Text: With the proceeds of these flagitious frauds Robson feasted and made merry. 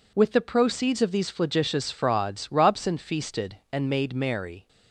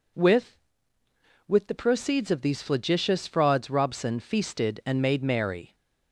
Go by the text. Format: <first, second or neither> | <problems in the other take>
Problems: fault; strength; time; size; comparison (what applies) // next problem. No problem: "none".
first | says "With" twice; at 1.4 s